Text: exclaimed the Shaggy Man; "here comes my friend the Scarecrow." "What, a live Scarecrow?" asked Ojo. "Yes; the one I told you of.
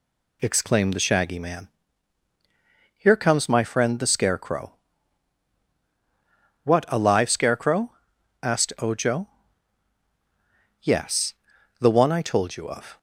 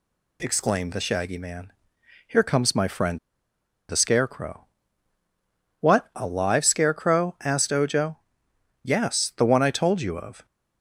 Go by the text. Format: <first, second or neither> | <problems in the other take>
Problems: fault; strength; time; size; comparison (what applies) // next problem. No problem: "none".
first | pauses between "friend" and "the"; noticeable; at 3.1 s; 0.70 s long